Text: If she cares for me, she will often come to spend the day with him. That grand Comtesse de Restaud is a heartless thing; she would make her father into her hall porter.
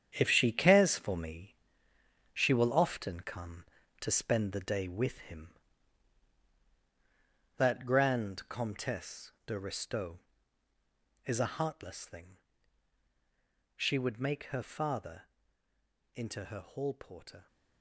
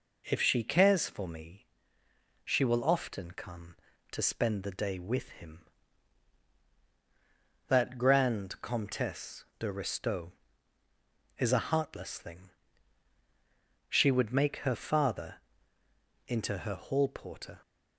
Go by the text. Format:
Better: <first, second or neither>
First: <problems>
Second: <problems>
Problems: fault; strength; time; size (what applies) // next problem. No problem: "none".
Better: second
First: gets quieter; strong; throughout; 10.5 dB // pauses between "father" and "into"; noticeable; at 15.2 s; 0.84 s long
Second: pauses between "father" and "into"; noticeable; at 15.4 s; 0.84 s long